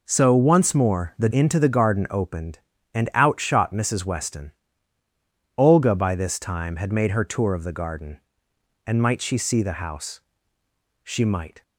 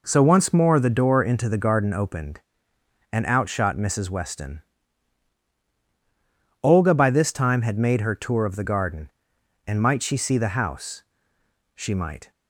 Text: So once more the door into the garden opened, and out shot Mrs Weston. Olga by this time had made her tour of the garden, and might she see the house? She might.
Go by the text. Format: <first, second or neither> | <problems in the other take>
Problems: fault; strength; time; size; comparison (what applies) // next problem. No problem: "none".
second | skips "door"; at 1.2 s